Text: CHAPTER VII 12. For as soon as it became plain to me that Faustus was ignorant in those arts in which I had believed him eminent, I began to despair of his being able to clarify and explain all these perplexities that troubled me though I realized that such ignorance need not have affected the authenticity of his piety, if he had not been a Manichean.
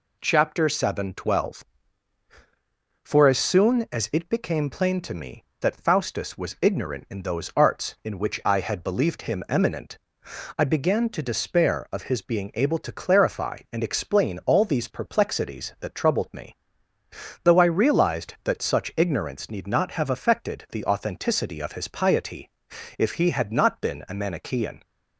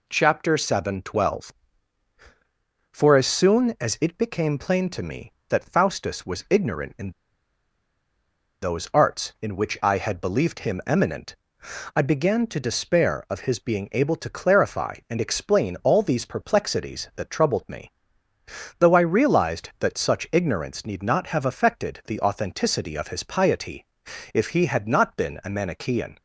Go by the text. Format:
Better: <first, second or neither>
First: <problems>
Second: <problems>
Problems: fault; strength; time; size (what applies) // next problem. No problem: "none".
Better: first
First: pauses between "me" and "though"; noticeable; at 16.5 s; 0.90 s long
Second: pauses between "in" and "those"; strong; at 7.1 s; 1.5 s long // pauses between "me" and "though"; noticeable; at 17.8 s; 0.90 s long